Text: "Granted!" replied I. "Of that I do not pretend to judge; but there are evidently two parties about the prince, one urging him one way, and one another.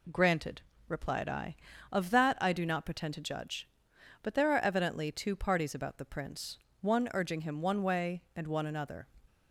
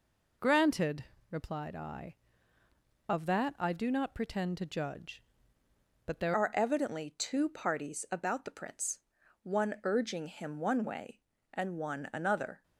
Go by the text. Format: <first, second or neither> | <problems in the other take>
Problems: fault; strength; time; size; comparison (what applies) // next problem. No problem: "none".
first | changes voice at "are"; from 6.3 s on; 6.3 s long